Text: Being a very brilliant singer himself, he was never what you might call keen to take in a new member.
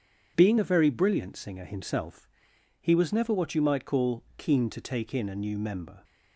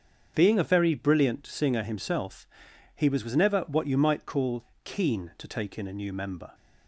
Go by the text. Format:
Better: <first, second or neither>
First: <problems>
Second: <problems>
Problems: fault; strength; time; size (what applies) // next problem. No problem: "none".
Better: first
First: starts louder than the rest; strong; until 1.3 s; 7.5 dB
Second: starts louder than the rest; strong; until 1.3 s; 7.5 dB // says "was" twice; at 3.2 s // pauses between "call" and "keen"; slight; at 4.6 s; 0.18 s long